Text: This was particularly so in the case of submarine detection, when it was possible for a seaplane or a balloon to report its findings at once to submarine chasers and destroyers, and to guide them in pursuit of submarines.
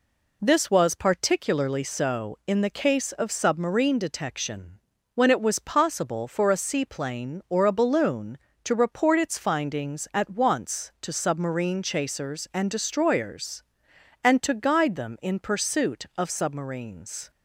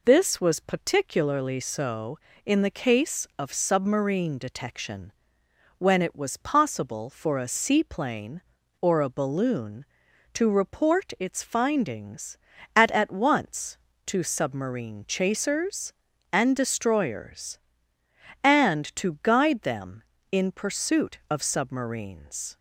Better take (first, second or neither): first